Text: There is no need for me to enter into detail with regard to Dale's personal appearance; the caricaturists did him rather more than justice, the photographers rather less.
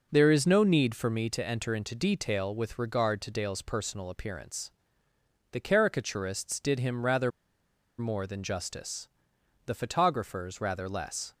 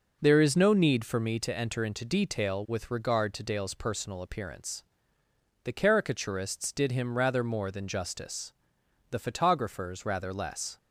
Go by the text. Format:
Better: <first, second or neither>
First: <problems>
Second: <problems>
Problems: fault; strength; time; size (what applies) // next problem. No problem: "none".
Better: second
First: pauses between "rather" and "more"; noticeable; at 7.3 s; 0.68 s long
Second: none